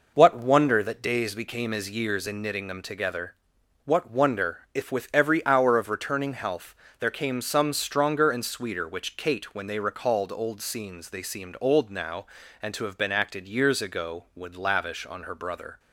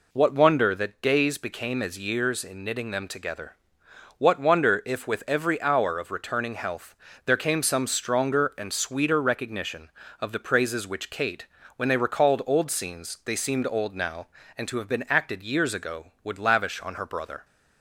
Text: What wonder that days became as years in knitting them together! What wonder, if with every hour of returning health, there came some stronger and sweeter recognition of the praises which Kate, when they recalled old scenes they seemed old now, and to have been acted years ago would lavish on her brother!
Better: second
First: skips "recognition of the praises"; at 8.8 s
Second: none

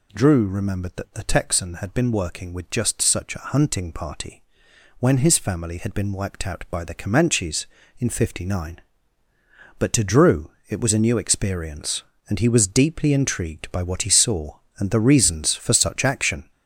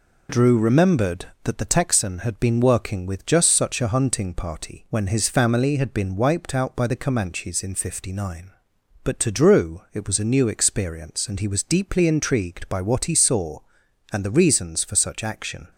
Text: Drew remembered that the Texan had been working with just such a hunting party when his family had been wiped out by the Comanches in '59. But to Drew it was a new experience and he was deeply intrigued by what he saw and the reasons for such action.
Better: second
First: gets louder; noticeable; throughout; 6 dB // pauses between "party" and "when"; noticeable; at 4.4 s; 0.56 s long // pauses between "Drew" and "it"; slight; at 10.5 s; 0.18 s long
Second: none

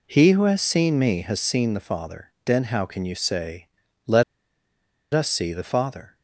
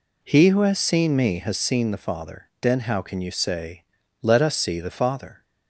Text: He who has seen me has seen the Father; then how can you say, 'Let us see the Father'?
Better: second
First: pauses between "Let" and "us"; noticeable; at 4.2 s; 0.90 s long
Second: none

